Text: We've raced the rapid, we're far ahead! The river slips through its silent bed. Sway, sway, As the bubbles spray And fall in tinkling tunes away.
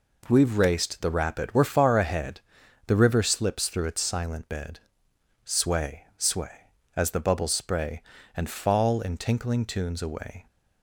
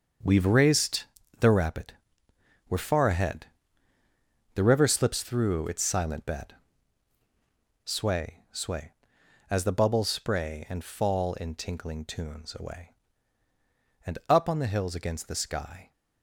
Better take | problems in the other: first | starts louder than the rest; until 1.5 s; 6.5 dB // pauses between "raced" and "the"; slight; at 1.0 s; 0.34 s long // goes on to say "And up on the hills against the sky"; strong; from 14.0 s on; 1.8 s long

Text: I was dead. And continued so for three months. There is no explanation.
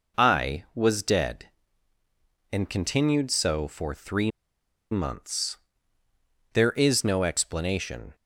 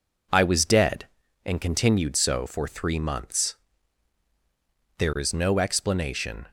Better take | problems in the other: second | pauses between "three" and "months"; noticeable; at 4.3 s; 0.60 s long

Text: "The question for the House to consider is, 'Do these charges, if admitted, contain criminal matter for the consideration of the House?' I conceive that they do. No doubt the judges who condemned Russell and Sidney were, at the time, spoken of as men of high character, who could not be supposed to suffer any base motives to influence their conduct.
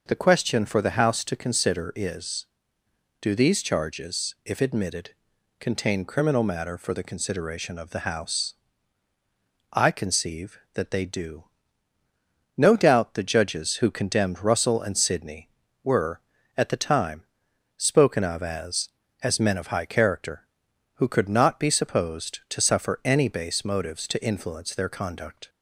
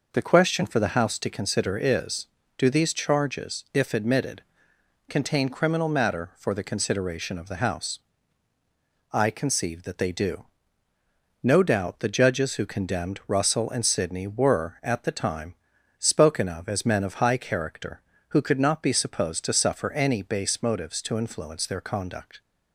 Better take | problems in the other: second | says "as" twice; at 19.2 s

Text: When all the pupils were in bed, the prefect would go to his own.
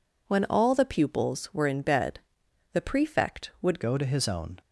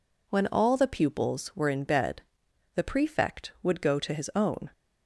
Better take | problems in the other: second | changes voice at "go"; from 3.8 s on; 0.8 s long

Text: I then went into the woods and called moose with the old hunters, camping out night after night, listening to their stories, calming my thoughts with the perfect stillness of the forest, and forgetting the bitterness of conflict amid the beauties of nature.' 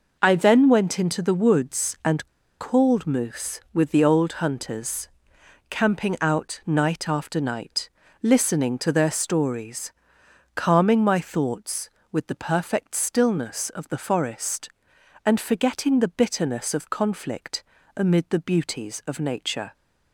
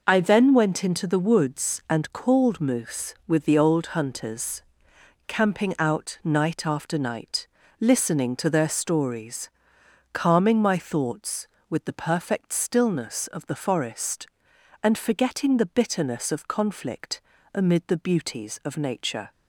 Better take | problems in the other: second | pauses between "and" and "called"; slight; at 2.2 s; 0.33 s long // pauses between "conflict" and "amid"; slight; at 17.6 s; 0.32 s long; slight in the second

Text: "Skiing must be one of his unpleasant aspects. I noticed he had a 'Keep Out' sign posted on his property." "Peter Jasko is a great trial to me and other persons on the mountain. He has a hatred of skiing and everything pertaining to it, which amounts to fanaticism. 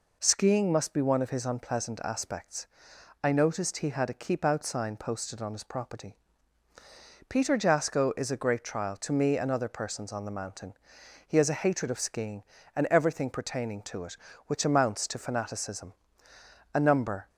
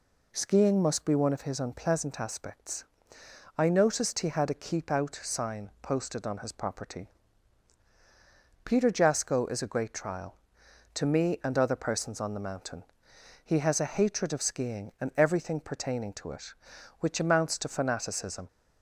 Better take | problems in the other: second | goes on to say "A number"; from 16.7 s on; 0.54 s long

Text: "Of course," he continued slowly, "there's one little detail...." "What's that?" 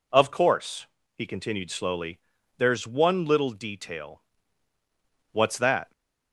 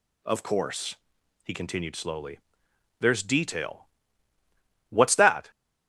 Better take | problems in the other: first | skips "one little"; at 3.2 s

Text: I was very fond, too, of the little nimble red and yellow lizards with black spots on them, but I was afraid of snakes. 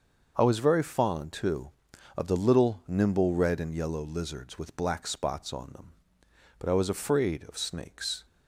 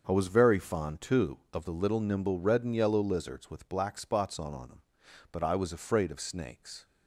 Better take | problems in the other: first | starts louder than the rest; until 1.0 s; 6.5 dB; also in the first // says "on" twice; at 4.5 s

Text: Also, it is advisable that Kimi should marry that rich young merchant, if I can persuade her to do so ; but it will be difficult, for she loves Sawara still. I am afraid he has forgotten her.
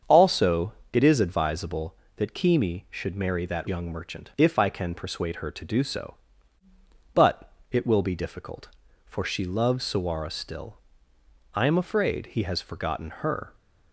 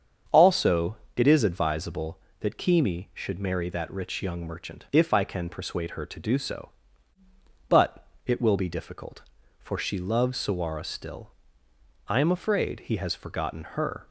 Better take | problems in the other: second | starts louder than the rest; strong; until 1.2 s; 7 dB; strong in the second // skips "rich"; at 3.6 s // pauses between "but" and "it"; slight; at 7.5 s; 0.20 s long; slight in the second

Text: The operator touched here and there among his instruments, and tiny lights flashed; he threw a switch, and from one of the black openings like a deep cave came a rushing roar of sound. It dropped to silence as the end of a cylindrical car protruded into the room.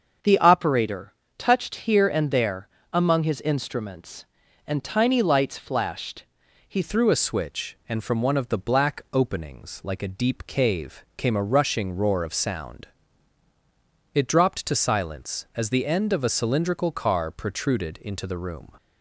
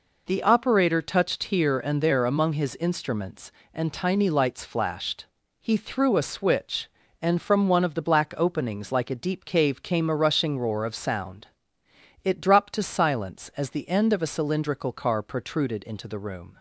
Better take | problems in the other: second | starts louder than the rest; until 1.4 s; 6.5 dB // pauses between "operator" and "touched"; slight; at 1.1 s; 0.24 s long // pauses between "there" and "among"; slight; at 2.6 s; 0.24 s long // changes voice at "threw"; from 6.8 s on; 11.9 s long

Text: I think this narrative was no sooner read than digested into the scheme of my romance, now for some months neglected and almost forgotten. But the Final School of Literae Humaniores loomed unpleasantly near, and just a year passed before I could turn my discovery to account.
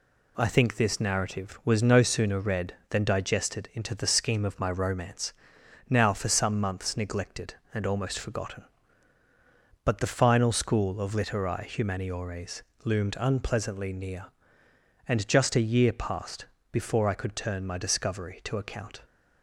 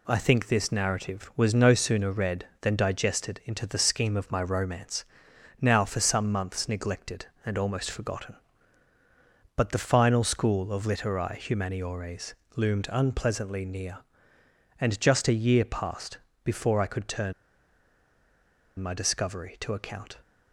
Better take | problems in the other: first | pauses between "Humaniores" and "loomed"; slight; at 12.3 s; 0.20 s long; slight in the first // pauses between "passed" and "before"; slight; at 16.1 s; 0.26 s long; slight in the first // pauses between "turn" and "my"; strong; at 17.3 s; 1.4 s long

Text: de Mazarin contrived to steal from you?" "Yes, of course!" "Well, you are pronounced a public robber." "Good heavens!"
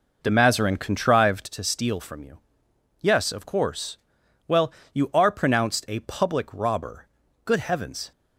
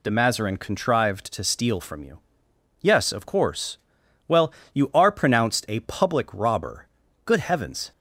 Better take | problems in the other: second | starts louder than the rest; noticeable; until 1.5 s; 5 dB

